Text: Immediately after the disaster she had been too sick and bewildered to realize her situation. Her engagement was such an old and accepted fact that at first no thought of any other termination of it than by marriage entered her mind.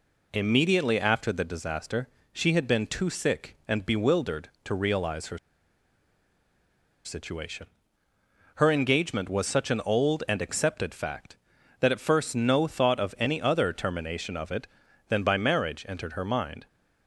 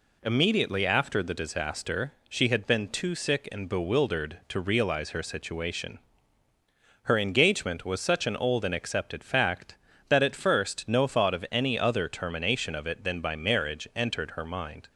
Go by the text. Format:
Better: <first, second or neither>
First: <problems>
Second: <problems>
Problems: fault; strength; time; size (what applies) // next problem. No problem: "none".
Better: second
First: pauses between "disaster" and "she"; slight; at 2.0 s; 0.26 s long // pauses between "her" and "situation"; strong; at 5.3 s; 1.6 s long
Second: pauses between "disaster" and "she"; slight; at 2.1 s; 0.16 s long